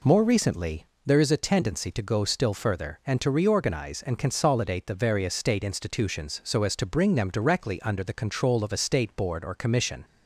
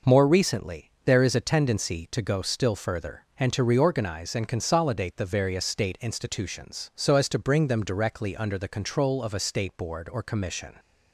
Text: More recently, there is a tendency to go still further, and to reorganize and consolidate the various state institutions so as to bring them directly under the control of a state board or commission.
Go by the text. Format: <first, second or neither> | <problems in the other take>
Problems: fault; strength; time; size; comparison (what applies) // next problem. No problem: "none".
neither | none